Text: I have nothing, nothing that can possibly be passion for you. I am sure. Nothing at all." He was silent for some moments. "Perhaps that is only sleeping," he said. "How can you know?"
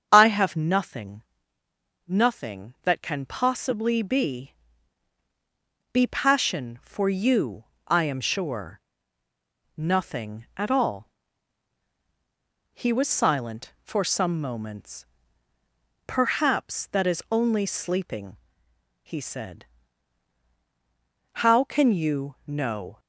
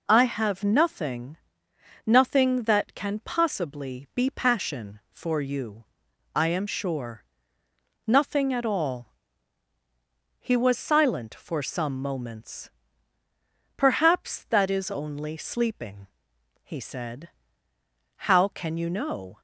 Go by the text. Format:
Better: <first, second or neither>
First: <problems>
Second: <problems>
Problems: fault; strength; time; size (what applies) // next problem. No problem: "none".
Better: second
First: starts louder than the rest; strong; until 1.1 s; 7.5 dB // says "be" twice; at 5.9 s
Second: none